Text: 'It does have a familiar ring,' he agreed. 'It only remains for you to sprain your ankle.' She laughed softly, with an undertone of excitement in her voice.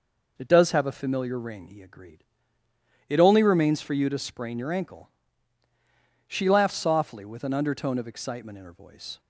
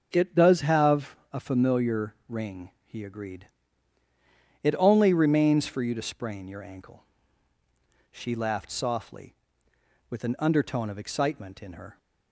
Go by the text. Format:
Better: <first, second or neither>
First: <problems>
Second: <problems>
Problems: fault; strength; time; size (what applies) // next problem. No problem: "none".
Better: first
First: none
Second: starts louder than the rest; noticeable; until 1.1 s; 6 dB // pauses between "have" and "a"; slight; at 1.1 s; 0.16 s long // stops before "voice"; at 11.9 s